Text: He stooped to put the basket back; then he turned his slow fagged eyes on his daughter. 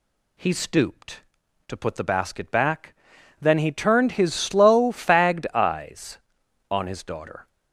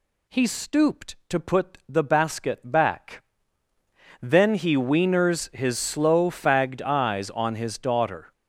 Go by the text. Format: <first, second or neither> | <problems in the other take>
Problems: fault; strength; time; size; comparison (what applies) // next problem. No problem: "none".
first | says "wieners" for "turned"; at 4.7 s